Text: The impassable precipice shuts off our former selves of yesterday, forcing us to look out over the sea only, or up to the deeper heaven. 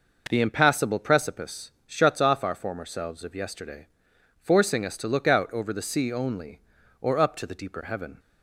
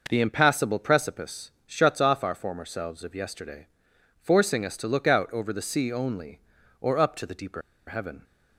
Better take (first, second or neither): first